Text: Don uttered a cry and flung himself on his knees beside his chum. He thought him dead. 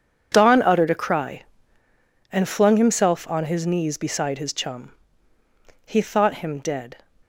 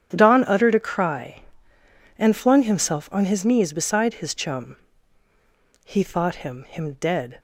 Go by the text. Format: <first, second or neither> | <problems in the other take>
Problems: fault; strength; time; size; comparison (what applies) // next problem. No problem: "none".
first | starts louder than the rest; strong; until 1.1 s; 9.5 dB // says "him" twice; at 6.6 s